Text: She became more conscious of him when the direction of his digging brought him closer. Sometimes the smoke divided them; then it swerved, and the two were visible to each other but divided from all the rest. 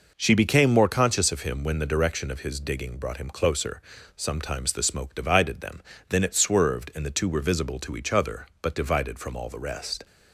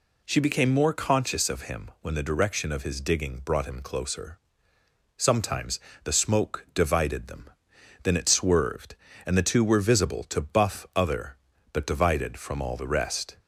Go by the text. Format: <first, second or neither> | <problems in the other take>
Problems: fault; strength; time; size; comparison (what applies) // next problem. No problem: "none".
first | pauses between "Sometimes" and "the"; slight; at 5.7 s; 0.24 s long // says "buff" for "each"; at 10.4 s